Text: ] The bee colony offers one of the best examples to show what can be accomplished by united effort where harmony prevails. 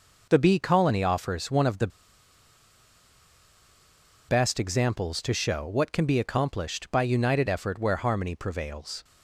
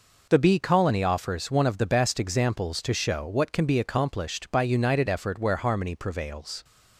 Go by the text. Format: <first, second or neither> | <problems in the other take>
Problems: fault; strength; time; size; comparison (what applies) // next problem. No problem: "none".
second | pauses between "the" and "best"; strong; at 1.8 s; 2.4 s long